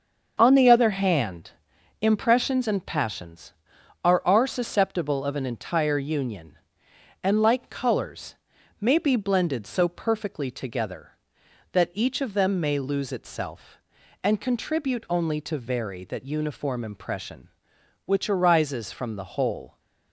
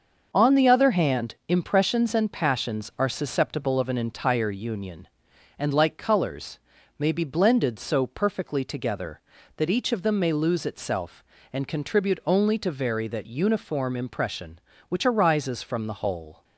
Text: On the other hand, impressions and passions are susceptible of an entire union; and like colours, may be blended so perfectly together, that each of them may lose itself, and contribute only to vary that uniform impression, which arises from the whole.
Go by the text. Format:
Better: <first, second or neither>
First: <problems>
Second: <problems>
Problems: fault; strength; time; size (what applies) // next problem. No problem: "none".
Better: second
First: starts louder than the rest; until 1.3 s; 7 dB // says "are" twice; at 4.2 s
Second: starts louder than the rest; until 1.3 s; 6.5 dB